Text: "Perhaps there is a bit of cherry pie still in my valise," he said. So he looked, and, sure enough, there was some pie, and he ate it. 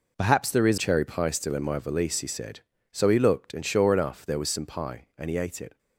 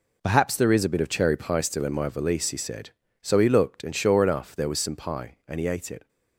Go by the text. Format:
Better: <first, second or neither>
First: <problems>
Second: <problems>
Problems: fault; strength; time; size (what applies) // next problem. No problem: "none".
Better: second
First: skips "a bit of"; at 0.7 s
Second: none